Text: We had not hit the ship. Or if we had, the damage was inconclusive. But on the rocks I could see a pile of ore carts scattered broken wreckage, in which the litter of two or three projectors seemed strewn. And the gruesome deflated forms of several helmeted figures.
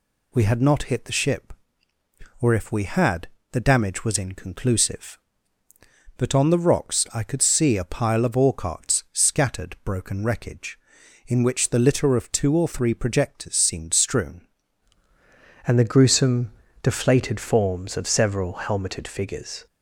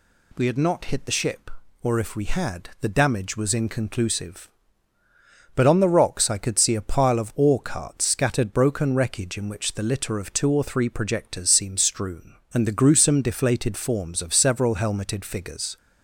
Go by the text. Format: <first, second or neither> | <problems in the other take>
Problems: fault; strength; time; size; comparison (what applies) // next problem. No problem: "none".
second | changes voice at "And"; from 15.6 s on; 4.0 s long // pauses between "gruesome" and "deflated"; slight; at 16.4 s; 0.32 s long